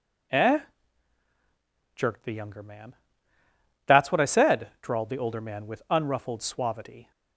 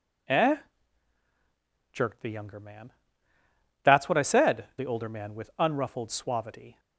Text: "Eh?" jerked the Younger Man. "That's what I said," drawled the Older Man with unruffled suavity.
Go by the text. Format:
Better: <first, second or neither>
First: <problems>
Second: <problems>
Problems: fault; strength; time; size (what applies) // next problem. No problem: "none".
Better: first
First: none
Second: skips "drawled"; at 4.7 s